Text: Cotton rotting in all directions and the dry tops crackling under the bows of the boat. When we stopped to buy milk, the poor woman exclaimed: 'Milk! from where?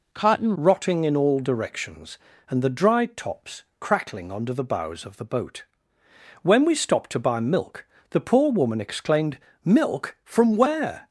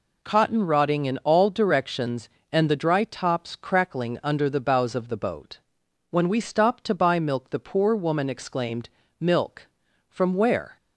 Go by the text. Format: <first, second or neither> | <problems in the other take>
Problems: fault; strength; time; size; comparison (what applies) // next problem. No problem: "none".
second | changes voice at "rotting"; from 0.5 s on; 10.5 s long // pauses between "tops" and "crackling"; slight; at 3.6 s; 0.16 s long